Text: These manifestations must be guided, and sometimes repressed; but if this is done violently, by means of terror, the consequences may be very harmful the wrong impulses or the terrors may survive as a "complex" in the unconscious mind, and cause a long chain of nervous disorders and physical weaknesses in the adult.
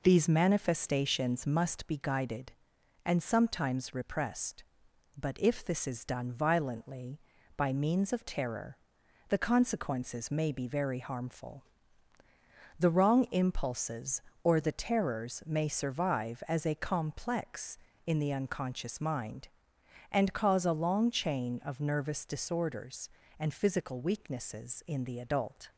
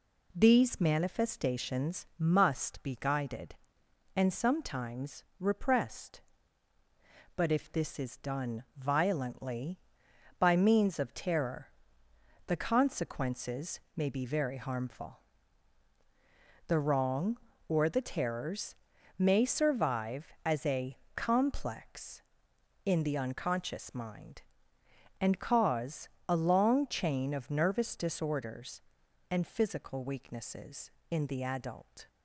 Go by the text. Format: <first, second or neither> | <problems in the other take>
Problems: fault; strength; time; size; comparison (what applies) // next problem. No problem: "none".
first | pauses between "sometimes" and "repressed"; slight; at 5.2 s; 0.18 s long // pauses between "consequences" and "may"; slight; at 13.8 s; 0.16 s long // pauses between "harmful" and "the"; strong; at 15.1 s; 1.4 s long; also in the first // skips "impulses"; at 17.5 s // pauses between "terrors" and "may"; at 18.7 s; 0.44 s long // pauses between "a" and "complex"; slight; at 20.9 s; 0.20 s long // pauses between "cause" and "a"; slight; at 26.0 s; 0.22 s long